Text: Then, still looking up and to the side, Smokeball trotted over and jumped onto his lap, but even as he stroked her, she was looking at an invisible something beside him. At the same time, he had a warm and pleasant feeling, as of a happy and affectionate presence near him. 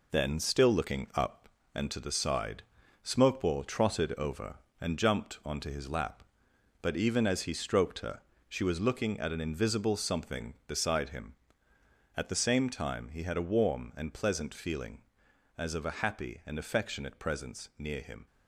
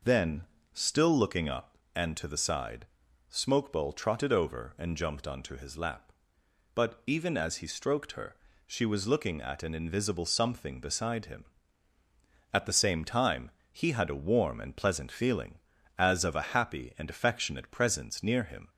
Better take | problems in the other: second | gets quieter; throughout; 6 dB

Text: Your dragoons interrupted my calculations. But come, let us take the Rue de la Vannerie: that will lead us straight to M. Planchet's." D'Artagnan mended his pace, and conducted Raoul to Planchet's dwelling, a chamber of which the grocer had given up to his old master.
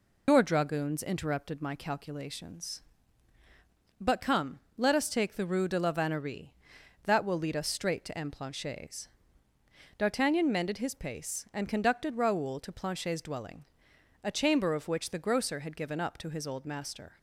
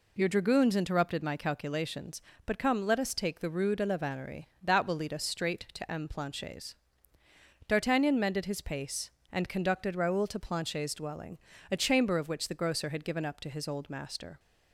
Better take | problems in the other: second | loses the start of "Your"; at 0.2 s; 115 ms

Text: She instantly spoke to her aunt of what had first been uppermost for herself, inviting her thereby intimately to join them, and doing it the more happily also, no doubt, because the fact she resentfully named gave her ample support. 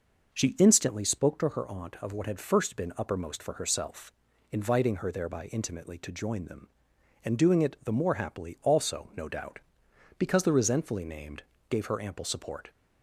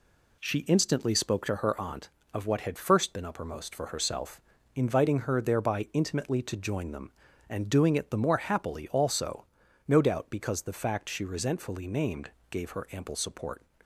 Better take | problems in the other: second | skips "fact she"; at 10.5 s // pauses between "named" and "gave"; slight; at 11.4 s; 0.26 s long; slight in the second

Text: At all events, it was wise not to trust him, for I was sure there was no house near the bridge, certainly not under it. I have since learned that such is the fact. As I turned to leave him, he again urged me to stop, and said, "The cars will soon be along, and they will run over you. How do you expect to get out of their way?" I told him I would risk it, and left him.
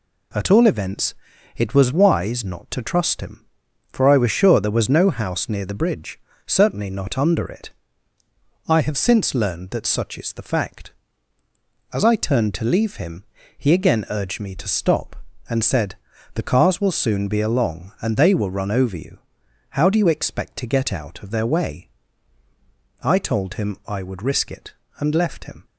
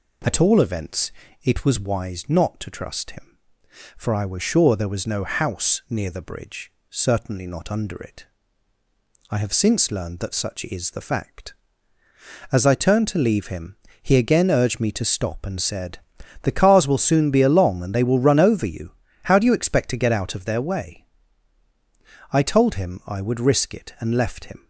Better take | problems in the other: neither | none

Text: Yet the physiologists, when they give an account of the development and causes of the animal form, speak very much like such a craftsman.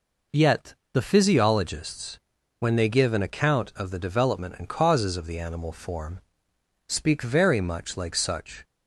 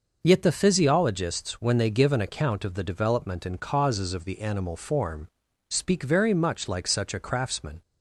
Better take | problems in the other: second | pauses between "Yet" and "the"; slight; at 0.7 s; 0.18 s long // stops before "a craftsman"; at 8.6 s

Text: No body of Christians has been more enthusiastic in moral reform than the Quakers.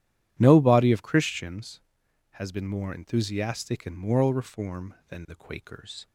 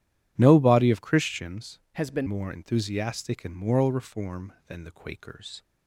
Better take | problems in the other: first | changes voice from "has" to "been"; from 1.9 to 2.2 s; 0.3 s long

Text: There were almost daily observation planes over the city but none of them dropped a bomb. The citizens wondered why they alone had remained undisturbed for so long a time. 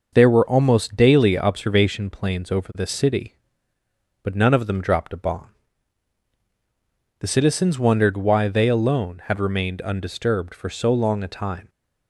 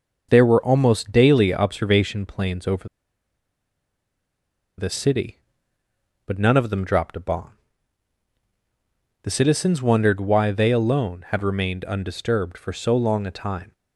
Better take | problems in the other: first | pauses between "over" and "the"; strong; at 2.8 s; 1.9 s long

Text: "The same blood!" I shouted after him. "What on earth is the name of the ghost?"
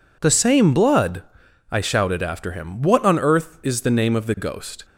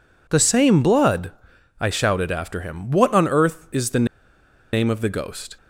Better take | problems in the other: first | pauses between "the" and "name"; noticeable; at 4.0 s; 0.67 s long

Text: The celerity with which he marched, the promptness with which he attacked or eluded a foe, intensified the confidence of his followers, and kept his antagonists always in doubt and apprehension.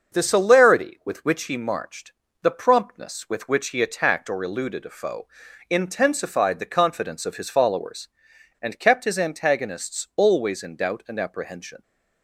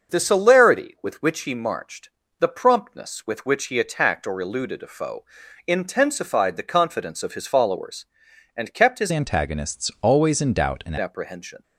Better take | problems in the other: first | starts louder than the rest; until 1.1 s; 6 dB; also in the first // changes voice from "antagonists" to "and"; from 9.1 to 10.9 s; 1.8 s long

